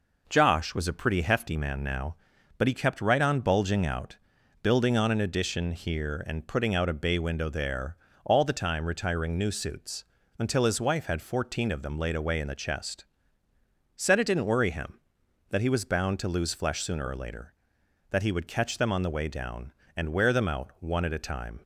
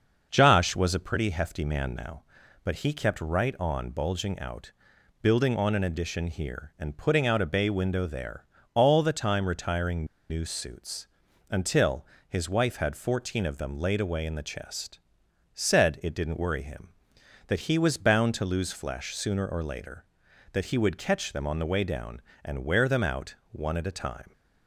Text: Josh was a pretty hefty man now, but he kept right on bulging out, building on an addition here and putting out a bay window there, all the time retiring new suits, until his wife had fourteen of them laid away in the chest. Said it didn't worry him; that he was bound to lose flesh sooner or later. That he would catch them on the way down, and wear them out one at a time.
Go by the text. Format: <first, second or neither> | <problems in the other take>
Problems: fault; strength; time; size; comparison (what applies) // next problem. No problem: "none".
first | starts louder than the rest; until 1.3 s; 6.5 dB // pauses between "retiring" and "new"; slight; at 10.0 s; 0.24 s long // pauses between "until" and "his"; slight; at 12.0 s; 0.24 s long // pauses between "out" and "one"; slight; at 23.3 s; 0.16 s long